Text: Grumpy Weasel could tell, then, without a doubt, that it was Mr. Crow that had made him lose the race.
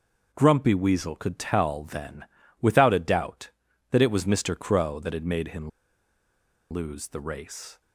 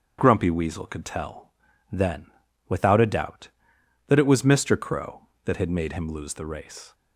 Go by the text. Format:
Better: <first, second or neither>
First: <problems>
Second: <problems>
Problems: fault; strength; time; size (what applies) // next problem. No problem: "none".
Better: second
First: starts louder than the rest; noticeable; until 1.3 s; 6 dB // pauses between "him" and "lose"; at 5.6 s; 1.0 s long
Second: starts louder than the rest; strong; until 1.2 s; 7.5 dB